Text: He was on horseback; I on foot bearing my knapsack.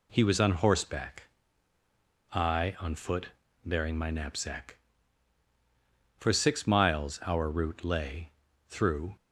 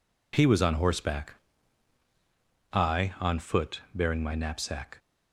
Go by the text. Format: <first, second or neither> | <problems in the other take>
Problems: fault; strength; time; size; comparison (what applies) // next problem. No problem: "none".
second | pauses between "foot" and "bearing"; at 3.2 s; 0.38 s long // goes on to say "For six miles our route lay through"; strong; from 6.1 s on; 2.9 s long